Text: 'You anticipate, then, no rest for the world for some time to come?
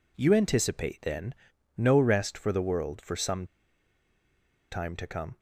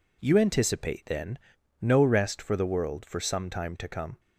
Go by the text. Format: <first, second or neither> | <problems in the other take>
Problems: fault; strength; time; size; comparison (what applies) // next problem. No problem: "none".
second | pauses between "some" and "time"; strong; at 3.4 s; 1.2 s long